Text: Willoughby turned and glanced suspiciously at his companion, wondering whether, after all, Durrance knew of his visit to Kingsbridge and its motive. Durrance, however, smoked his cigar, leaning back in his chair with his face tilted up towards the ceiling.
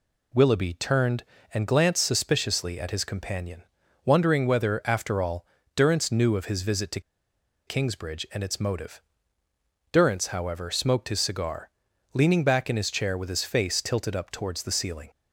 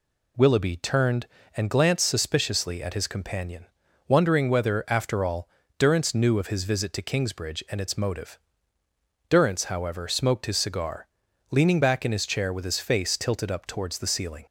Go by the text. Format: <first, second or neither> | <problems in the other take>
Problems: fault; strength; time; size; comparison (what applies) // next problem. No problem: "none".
second | pauses between "to" and "Kingsbridge"; noticeable; at 6.9 s; 0.67 s long